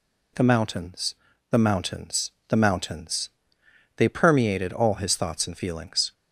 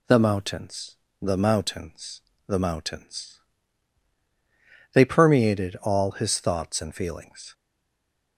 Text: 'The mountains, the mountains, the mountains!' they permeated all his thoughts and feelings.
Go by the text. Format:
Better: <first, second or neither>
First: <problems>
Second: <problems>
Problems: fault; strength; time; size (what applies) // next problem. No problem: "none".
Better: first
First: none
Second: stays silent after the last word; slight; from 7.5 s on; 0.8 s long